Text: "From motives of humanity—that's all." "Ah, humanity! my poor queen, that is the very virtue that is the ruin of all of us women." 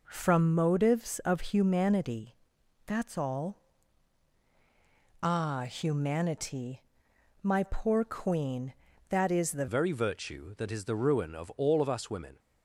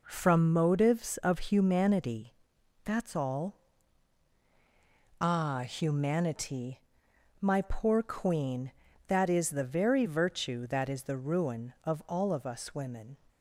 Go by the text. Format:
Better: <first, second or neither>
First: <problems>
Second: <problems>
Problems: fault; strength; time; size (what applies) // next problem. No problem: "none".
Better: second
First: changes voice at "very"; from 9.6 s on; 2.7 s long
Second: none